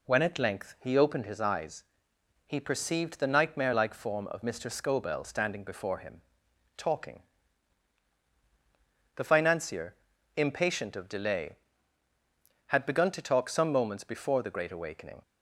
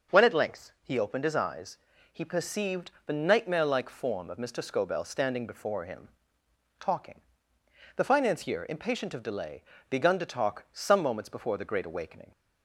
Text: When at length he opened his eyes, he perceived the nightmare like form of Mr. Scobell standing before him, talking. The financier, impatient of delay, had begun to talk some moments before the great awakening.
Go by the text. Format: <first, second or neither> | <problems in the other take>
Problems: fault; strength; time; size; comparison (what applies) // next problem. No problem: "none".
first | skips "had"; at 9.7 s